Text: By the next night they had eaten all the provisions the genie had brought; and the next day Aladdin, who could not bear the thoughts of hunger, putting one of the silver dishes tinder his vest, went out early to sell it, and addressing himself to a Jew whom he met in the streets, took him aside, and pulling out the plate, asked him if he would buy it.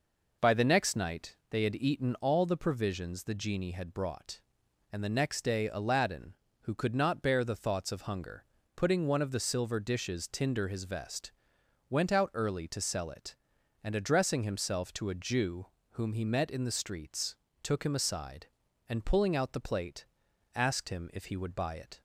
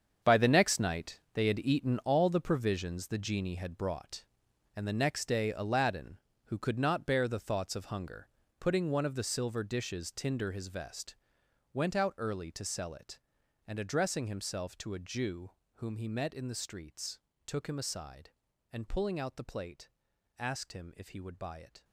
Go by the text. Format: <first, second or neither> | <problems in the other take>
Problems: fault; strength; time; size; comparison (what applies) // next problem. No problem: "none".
first | gets quieter; strong; throughout; 12 dB // pauses between "Jew" and "whom"; slight; at 15.5 s; 0.23 s long; slight in the first